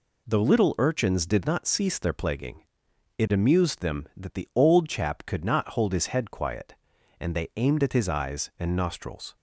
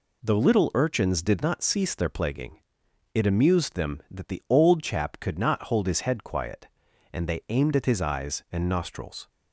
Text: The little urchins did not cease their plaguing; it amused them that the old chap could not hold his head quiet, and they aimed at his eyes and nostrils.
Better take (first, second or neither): neither